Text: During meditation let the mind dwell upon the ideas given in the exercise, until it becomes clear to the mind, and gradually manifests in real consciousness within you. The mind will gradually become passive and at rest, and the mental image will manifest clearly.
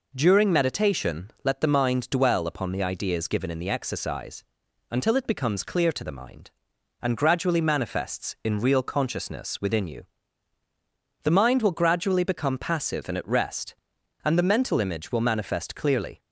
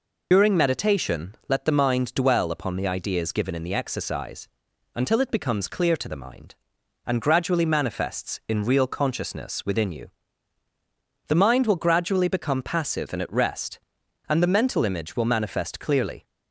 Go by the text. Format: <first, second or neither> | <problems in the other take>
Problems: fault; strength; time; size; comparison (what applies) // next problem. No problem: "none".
first | loses the start of "During"; at 0.3 s; 125 ms